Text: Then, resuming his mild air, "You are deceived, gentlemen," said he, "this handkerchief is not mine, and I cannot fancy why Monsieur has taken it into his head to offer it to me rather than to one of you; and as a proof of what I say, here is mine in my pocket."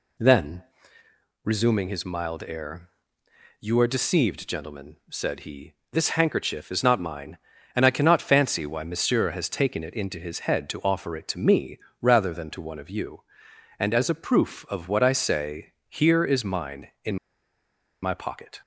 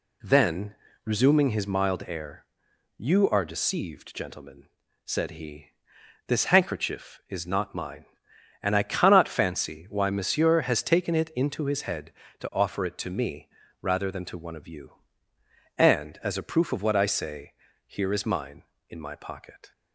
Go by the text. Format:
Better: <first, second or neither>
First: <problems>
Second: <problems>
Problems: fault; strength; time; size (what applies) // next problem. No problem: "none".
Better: second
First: pauses between "me" and "rather"; slight; at 11.7 s; 0.24 s long // pauses between "in" and "my"; noticeable; at 17.1 s; 0.87 s long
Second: pauses between "me" and "rather"; slight; at 13.4 s; 0.32 s long